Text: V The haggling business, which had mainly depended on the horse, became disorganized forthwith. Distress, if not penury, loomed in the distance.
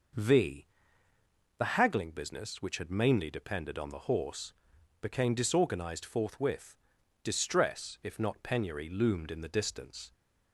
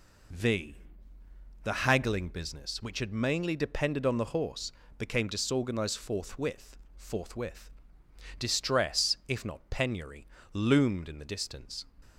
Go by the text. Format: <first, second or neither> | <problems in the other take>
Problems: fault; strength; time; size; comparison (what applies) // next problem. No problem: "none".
first | pauses between "V" and "The"; noticeable; at 0.7 s; 0.86 s long; noticeable in the first // says "forthwith" twice; at 6.9 s